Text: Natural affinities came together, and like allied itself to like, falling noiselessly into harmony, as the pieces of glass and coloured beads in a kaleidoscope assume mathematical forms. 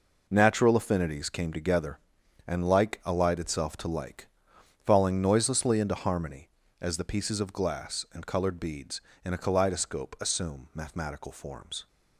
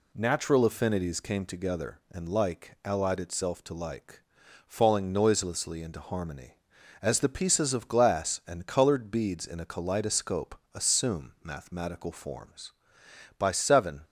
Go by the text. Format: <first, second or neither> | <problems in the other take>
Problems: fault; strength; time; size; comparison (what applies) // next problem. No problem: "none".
first | pauses between "kaleidoscope" and "assume"; slight; at 10.5 s; 0.20 s long // goes on to say "By seven"; noticeable; from 13.3 s on; 0.64 s long